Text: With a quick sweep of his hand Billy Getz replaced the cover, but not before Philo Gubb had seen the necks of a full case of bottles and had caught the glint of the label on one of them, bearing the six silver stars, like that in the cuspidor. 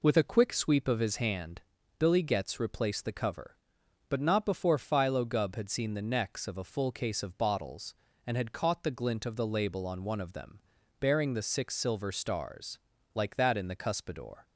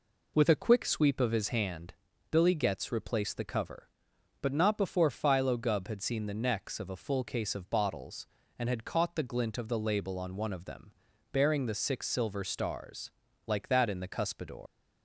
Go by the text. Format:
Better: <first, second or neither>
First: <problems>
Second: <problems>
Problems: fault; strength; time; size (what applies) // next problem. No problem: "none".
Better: first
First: pauses between "hand" and "Billy"; at 1.6 s; 0.38 s long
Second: pauses between "hand" and "Billy"; at 1.9 s; 0.38 s long // leaves "cuspidor" unfinished; at 14.6 s; 120 ms